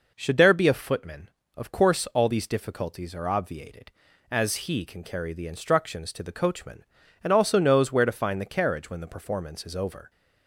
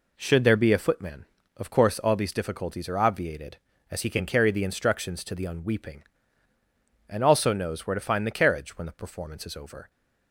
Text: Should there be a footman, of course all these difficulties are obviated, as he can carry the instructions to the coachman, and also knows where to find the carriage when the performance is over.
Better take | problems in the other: first | says "unweeping" for "coachman"; at 5.4 s

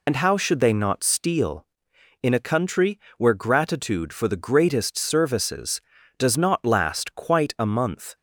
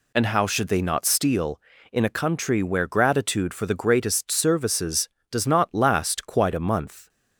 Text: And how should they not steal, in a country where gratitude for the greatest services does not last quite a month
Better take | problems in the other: second | loses the start of "And"; at 0.0 s; 65 ms // pauses between "country" and "where"; slight; at 2.9 s; 0.18 s long

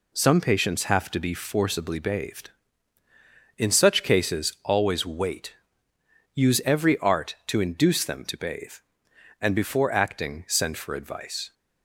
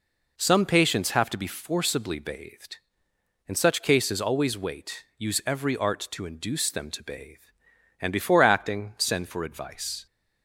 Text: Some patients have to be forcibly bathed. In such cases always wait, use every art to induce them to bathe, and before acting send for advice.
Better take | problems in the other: neither | none

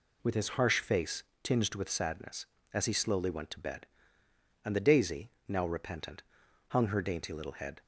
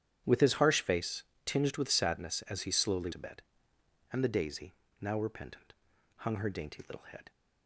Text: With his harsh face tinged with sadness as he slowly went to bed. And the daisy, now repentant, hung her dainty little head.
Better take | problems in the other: first | starts louder than the rest; strong; until 1.4 s; 10.5 dB // pauses between "face" and "tinged"; slight; at 1.2 s; 0.22 s long; slight in the first // skips "went"; at 3.1 s

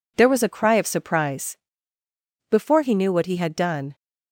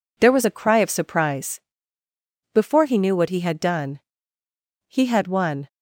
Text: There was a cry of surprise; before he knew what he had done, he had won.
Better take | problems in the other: second | stops before "he had won"; at 3.9 s

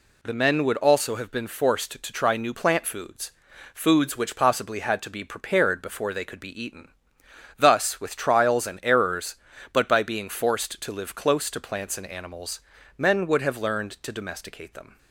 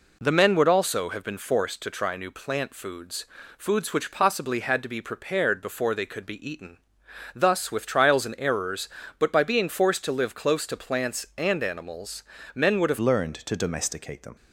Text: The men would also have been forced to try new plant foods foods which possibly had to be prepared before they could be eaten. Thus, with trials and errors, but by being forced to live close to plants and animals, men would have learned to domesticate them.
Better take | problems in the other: first | pauses between "foods" and "foods"; slight; at 3.2 s; 0.32 s long; also in the first // changes voice at "learned"; from 12.9 s on; 1.4 s long

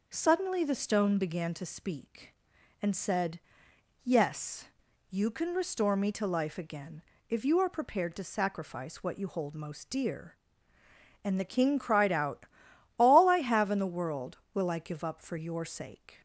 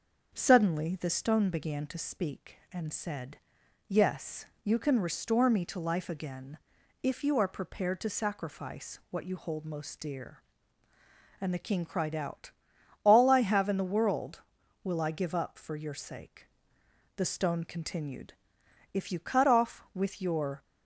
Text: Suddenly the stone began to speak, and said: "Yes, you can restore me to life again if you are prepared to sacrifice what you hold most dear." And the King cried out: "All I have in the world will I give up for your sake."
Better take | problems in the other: first | starts louder than the rest; until 1.3 s; 6.5 dB // pauses between "again" and "if"; noticeable; at 6.5 s; 0.46 s long; slight in the first // goes on to say "The stone continued If you cut off with your"; strong; from 17.1 s on; 3.4 s long

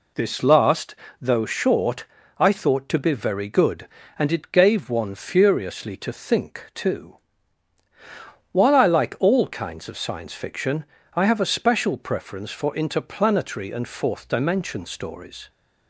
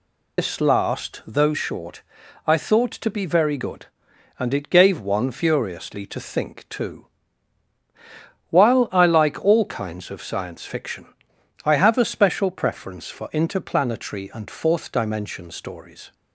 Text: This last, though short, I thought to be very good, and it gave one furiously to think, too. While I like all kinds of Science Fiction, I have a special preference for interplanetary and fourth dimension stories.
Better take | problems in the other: first | loses the start of "This"; at 0.3 s; 115 ms

